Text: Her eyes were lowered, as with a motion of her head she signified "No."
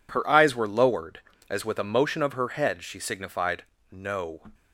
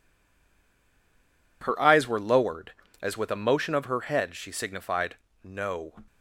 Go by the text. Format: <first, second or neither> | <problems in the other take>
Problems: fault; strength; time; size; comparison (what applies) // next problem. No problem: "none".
first | stays silent before the first word; noticeable; until 1.6 s; 1.6 s long // pauses between "signified" and "No"; slight; at 5.1 s; 0.30 s long; slight in the first